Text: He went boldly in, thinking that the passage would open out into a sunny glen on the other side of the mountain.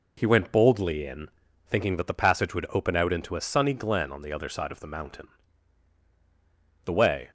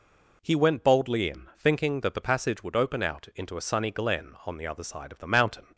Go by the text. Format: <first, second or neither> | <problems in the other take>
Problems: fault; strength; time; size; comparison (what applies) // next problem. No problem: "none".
second | goes on to say "The way"; slight; from 6.8 s on; 0.42 s long